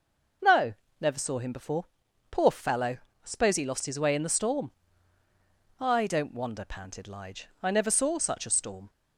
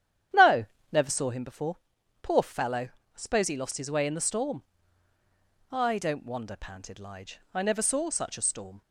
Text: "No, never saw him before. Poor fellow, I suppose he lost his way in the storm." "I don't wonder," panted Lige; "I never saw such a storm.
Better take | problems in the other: first | starts louder than the rest; strong; until 1.4 s; 9.5 dB

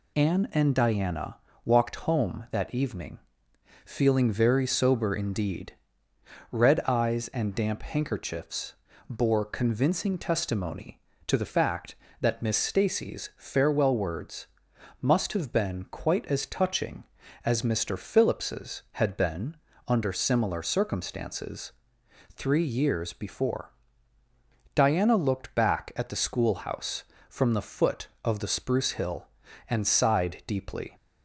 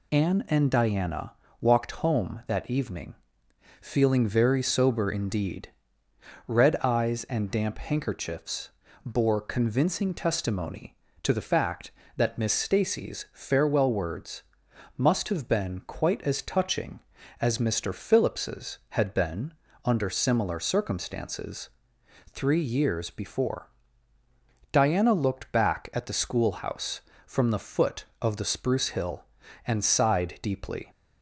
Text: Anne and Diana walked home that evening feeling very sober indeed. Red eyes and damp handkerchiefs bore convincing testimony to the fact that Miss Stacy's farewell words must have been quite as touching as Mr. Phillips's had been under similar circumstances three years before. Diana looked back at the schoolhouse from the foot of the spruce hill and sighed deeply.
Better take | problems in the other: neither | pauses between "Diana" and "walked"; slight; the same in both // pauses between "evening" and "feeling"; noticeable; the same in both // pauses between "handkerchiefs" and "bore"; slight; the same in both // pauses between "words" and "must"; noticeable; the same in both // pauses between "been" and "under"; slight; the same in both // pauses between "circumstances" and "three"; noticeable; the same in both

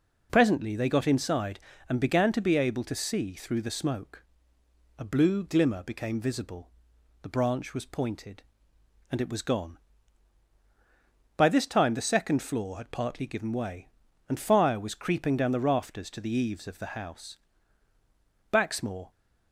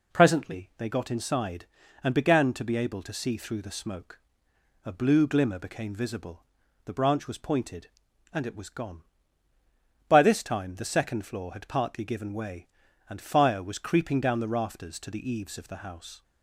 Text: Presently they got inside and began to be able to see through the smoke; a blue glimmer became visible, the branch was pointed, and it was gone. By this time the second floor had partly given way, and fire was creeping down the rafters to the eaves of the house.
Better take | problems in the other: second | goes on to say "Baxmore"; from 18.5 s on; 0.58 s long

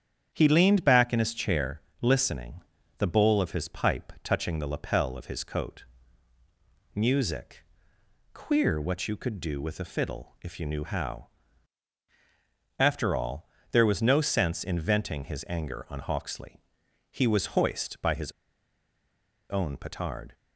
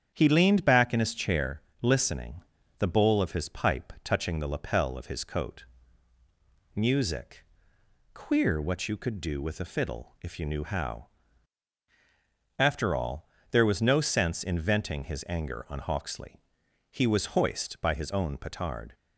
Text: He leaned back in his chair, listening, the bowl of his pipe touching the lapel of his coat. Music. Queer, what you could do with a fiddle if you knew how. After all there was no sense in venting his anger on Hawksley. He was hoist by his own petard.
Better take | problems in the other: second | starts louder than the rest; strong; until 1.3 s; 9 dB; strong in the second // pauses between "all" and "there"; slight; at 13.4 s; 0.24 s long; slight in the second // pauses between "his" and "own"; at 18.2 s; 1.1 s long

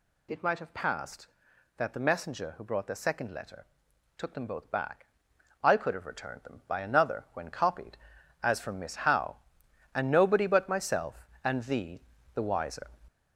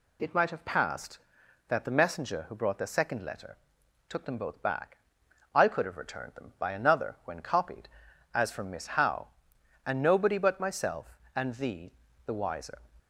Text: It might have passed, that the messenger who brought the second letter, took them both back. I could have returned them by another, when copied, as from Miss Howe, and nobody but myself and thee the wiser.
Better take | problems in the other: second | gets louder; noticeable; throughout; 5.5 dB // pauses between "thee" and "the"; slight; at 12.0 s; 0.34 s long; slight in the second

